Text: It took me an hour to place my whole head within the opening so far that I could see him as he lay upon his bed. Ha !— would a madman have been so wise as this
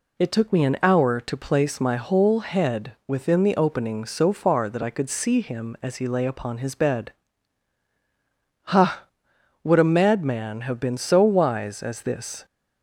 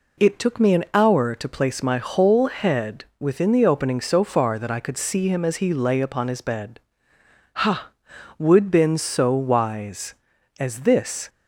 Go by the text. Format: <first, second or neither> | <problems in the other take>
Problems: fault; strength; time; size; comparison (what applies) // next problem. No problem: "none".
first | pauses between "head" and "within"; slight; at 3.0 s; 0.16 s long // skips "a madman have"; at 8.6 s